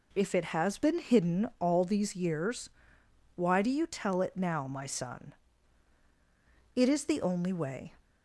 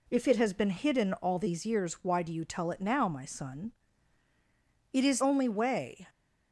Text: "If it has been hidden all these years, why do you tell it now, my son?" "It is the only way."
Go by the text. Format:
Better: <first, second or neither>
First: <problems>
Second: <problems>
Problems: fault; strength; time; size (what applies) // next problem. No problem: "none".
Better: first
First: none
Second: skips "the"; at 5.1 s